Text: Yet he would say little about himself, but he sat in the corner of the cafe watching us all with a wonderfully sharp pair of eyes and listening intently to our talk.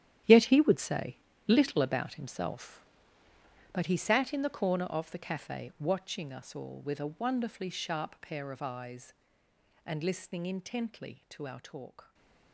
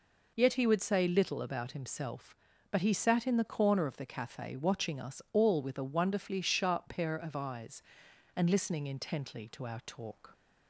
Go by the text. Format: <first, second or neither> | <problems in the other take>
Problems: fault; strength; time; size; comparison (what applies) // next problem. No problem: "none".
second | gets quieter; strong; throughout; 13.5 dB // pauses between "say" and "little"; slight; at 1.1 s; 0.30 s long // stays silent after the last word; slight; from 12.0 s on; 0.5 s long